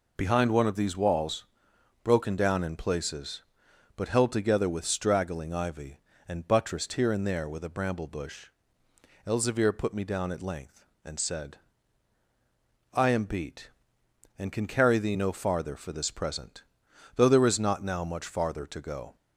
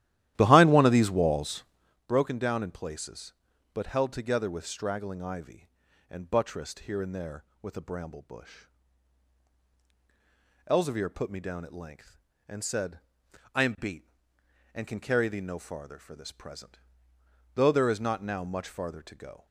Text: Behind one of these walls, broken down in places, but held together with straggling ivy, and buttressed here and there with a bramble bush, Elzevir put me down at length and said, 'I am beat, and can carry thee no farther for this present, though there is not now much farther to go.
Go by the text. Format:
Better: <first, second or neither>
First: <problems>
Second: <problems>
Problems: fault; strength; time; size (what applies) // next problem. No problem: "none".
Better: first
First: none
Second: starts louder than the rest; strong; until 2.0 s; 13.5 dB